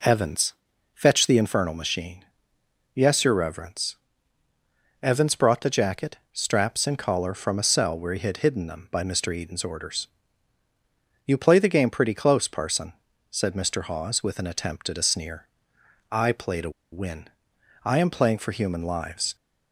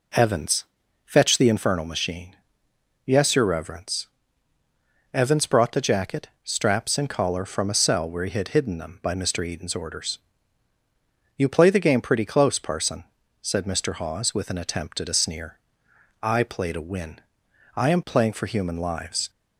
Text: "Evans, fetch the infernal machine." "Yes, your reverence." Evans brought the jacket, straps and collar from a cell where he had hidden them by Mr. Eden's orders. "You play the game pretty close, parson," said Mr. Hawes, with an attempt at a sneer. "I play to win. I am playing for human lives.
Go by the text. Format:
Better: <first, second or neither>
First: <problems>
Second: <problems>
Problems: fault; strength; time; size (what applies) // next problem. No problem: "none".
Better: second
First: pauses between "to" and "win"; slight; at 16.6 s; 0.22 s long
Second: none